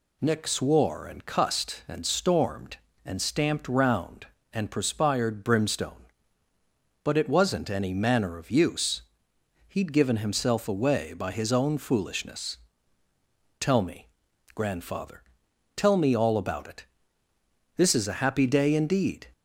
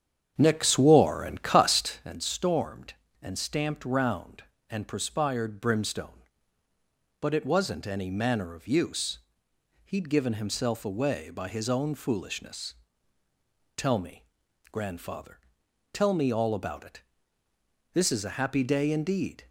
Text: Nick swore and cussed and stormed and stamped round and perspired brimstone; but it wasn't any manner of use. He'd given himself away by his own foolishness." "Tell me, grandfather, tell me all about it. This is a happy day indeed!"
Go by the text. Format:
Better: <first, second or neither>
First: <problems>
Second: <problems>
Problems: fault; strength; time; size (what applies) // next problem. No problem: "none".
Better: first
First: none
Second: starts louder than the rest; strong; until 2.2 s; 8.5 dB